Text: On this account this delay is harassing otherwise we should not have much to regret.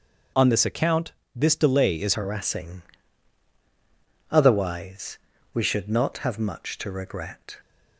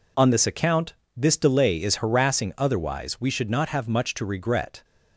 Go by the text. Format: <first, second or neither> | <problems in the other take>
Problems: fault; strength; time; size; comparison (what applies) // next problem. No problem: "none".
second | pauses between "account" and "this"; slight; at 1.1 s; 0.24 s long; slight in the second // changes voice at "harassing"; from 2.1 s on; 5.4 s long // pauses between "harassing" and "otherwise"; strong; at 2.8 s; 1.5 s long // pauses between "otherwise" and "we"; slight; at 5.1 s; 0.34 s long